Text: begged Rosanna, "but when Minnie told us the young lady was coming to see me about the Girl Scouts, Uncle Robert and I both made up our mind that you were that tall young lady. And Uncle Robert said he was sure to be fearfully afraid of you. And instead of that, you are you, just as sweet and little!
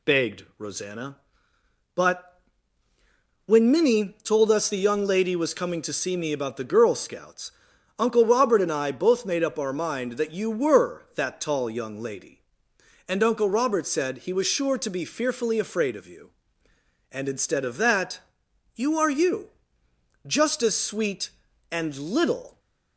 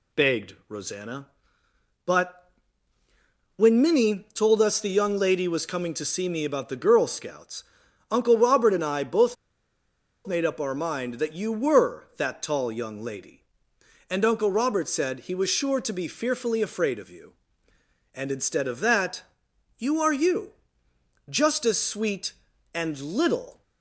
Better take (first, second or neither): first